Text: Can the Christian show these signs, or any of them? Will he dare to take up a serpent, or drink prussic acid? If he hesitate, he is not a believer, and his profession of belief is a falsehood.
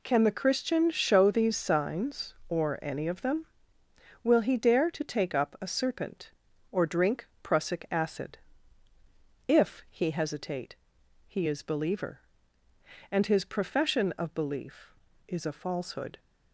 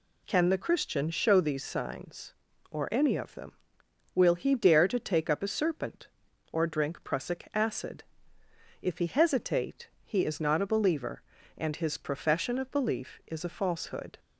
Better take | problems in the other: second | pauses between "drink" and "prussic"; slight; at 7.2 s; 0.16 s long // skips "not a"; at 11.6 s

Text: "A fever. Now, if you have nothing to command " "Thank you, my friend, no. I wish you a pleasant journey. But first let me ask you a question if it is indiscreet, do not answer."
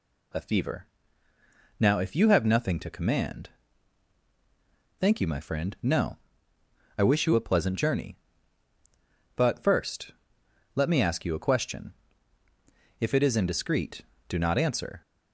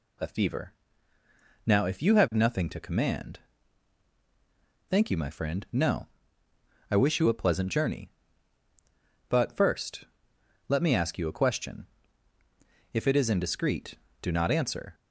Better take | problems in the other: neither | pauses between "first" and "let"; noticeable; the same in both // pauses between "question" and "if"; the same in both

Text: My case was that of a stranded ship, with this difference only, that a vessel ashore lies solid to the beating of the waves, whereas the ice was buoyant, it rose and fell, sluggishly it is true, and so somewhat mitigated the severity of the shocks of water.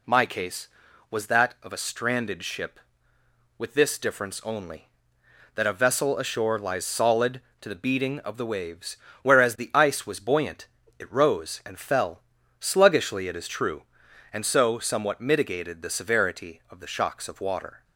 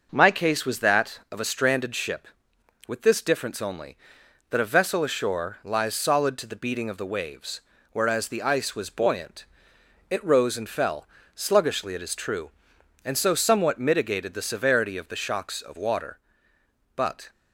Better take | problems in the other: first | goes on to say "But"; slight; from 16.9 s on; 0.34 s long

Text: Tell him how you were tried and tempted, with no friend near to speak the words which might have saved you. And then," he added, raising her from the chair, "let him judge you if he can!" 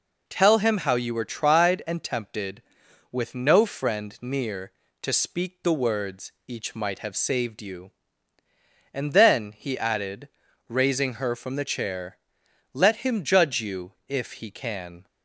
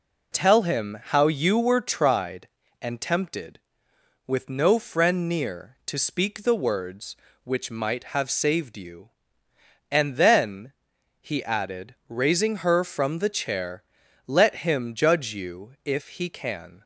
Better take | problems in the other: second | says "each" for "which"; at 6.4 s // pauses between "you" and "if"; slight; at 13.9 s; 0.16 s long

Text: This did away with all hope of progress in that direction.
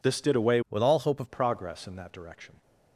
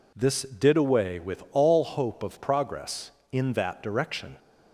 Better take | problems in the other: second | changes voice from "with" to "of"; from 0.6 to 1.2 s; 0.6 s long

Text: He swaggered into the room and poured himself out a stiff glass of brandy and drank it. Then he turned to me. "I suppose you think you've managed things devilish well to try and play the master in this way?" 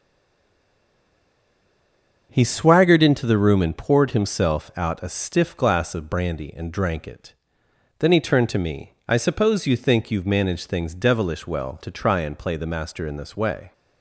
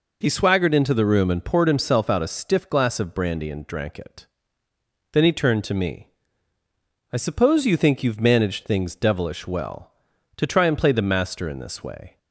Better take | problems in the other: second | stays silent before the first word; until 2.3 s; 2.3 s long // starts louder than the rest; until 3.3 s; 6.5 dB

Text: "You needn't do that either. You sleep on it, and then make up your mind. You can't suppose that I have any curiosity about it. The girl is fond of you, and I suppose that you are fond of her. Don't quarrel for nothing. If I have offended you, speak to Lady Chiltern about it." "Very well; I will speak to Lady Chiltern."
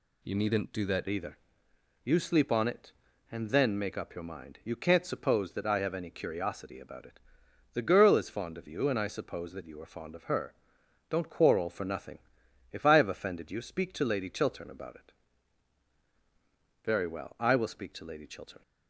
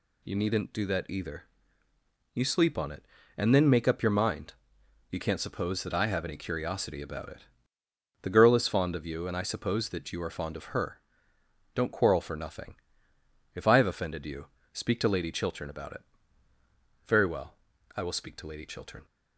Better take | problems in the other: second | changes voice at "either"; from 1.0 s on; 17.6 s long

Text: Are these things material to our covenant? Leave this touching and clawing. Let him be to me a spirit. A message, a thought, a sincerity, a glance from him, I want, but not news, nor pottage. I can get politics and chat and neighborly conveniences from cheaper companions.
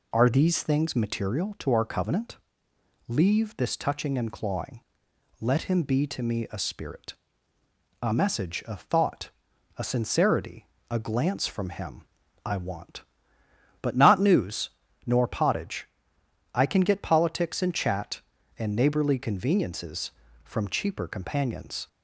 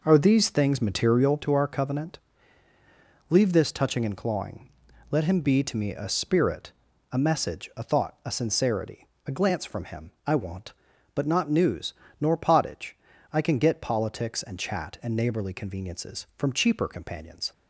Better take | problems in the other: first | starts louder than the rest; noticeable; until 1.7 s; 5 dB

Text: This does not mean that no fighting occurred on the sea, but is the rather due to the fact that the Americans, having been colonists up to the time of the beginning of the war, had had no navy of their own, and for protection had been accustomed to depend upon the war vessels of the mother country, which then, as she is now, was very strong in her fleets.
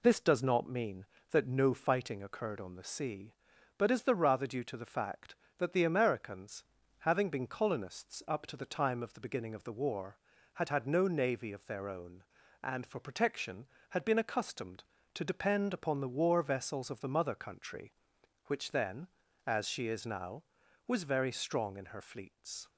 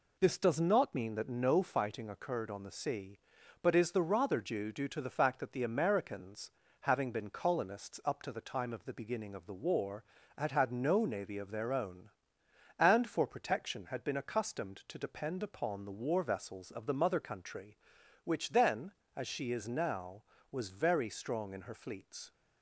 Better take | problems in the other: first | says "due" twice; at 4.7 s

